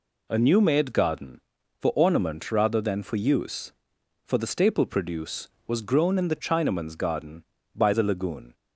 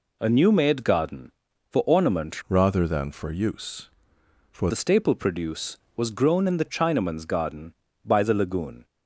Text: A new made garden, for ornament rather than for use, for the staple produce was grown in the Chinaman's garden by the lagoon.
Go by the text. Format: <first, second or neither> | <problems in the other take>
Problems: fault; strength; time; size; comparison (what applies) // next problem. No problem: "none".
first | changes voice from "rather" to "for"; from 2.4 to 4.6 s; 2.2 s long